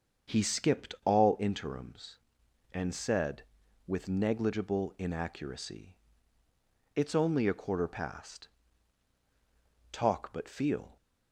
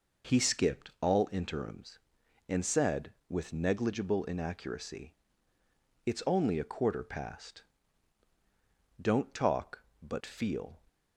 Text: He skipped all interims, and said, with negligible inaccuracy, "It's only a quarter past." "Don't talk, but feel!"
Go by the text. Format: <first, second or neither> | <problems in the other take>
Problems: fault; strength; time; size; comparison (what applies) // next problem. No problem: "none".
second | starts louder than the rest; until 1.4 s; 7 dB // skips "Don't"; at 9.1 s